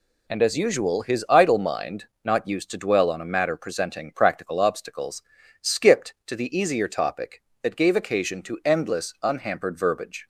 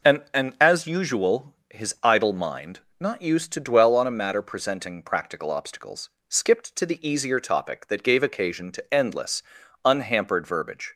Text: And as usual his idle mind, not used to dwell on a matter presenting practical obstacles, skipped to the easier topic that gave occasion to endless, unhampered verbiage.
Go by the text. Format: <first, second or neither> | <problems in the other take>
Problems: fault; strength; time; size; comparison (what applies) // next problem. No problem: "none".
first | says "And" twice; at 0.3 s // pauses between "usual" and "his"; slight; at 1.5 s; 0.16 s long